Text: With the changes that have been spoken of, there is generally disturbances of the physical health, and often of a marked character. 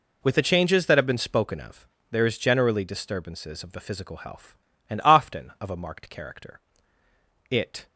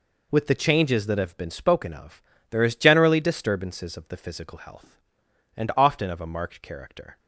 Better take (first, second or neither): second